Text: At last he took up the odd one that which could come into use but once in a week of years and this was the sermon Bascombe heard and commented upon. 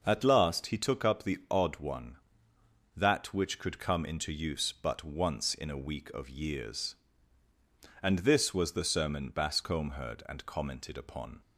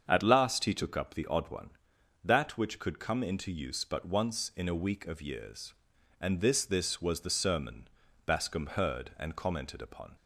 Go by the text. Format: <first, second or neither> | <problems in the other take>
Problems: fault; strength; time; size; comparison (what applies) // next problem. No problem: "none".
first | starts louder than the rest; until 1.0 s; 7 dB // says "this" twice; at 6.6 s // pauses between "sermon" and "Bascombe"; at 7.8 s; 0.38 s long